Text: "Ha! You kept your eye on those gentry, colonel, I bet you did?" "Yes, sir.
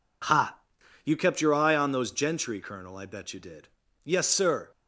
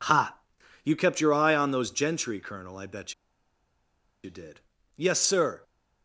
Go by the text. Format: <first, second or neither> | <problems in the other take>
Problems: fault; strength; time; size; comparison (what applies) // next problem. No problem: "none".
first | pauses between "bet" and "you"; at 3.1 s; 1.1 s long